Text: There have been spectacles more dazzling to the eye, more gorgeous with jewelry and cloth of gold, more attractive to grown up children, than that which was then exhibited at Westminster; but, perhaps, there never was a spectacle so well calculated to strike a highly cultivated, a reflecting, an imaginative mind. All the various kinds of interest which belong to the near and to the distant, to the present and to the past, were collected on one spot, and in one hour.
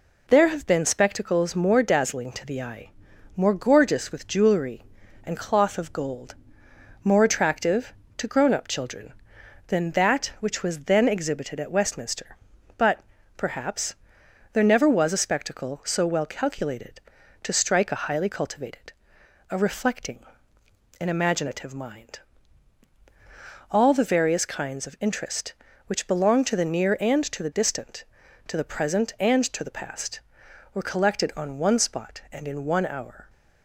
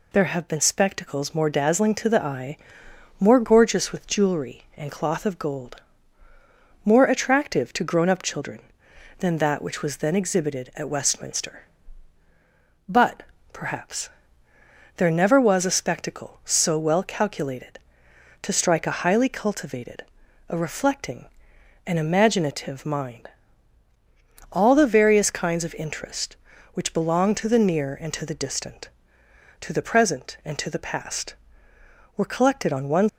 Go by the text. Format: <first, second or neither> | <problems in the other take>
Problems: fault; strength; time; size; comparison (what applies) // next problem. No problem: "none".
first | stops before "spot and in one hour"; at 33.0 s